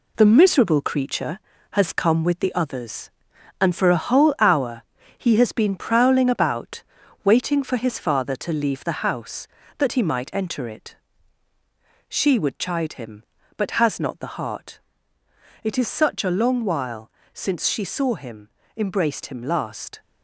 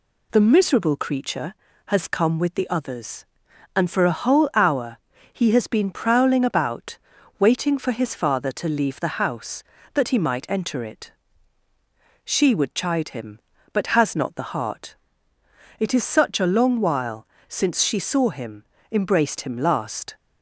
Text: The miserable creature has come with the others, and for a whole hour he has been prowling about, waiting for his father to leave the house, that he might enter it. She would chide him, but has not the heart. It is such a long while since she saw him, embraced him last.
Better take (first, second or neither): second